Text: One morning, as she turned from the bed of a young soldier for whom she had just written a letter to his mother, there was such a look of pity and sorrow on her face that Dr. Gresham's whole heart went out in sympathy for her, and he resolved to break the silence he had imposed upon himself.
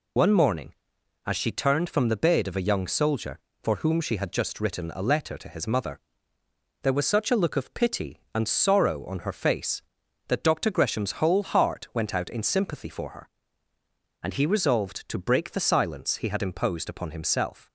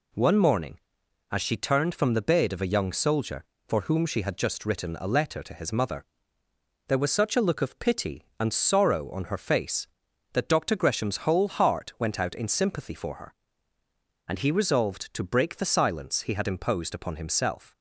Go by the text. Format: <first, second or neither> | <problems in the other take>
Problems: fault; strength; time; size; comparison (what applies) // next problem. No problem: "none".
second | loses the start of "One"; at 0.1 s; 75 ms